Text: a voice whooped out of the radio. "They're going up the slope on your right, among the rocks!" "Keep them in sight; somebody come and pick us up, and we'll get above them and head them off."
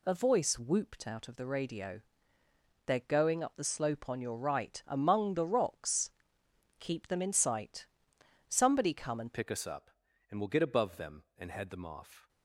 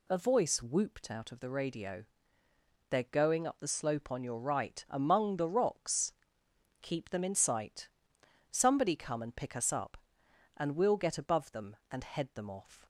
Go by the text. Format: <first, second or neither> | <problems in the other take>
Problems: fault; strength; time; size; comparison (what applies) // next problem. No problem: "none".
second | changes voice at "pick"; from 9.3 s on; 2.9 s long